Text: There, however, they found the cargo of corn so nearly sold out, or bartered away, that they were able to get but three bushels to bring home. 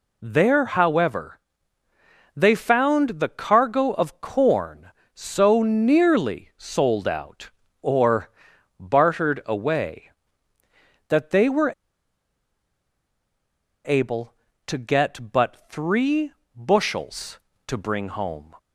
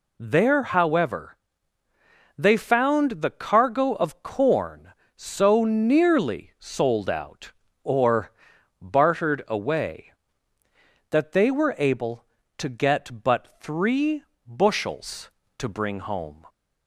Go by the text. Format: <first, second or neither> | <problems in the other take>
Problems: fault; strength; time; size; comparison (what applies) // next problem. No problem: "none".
second | pauses between "or" and "bartered"; noticeable; at 8.2 s; 0.50 s long; noticeable in the second // pauses between "were" and "able"; strong; at 11.7 s; 2.1 s long // pauses between "three" and "bushels"; slight; at 16.3 s; 0.24 s long; slight in the second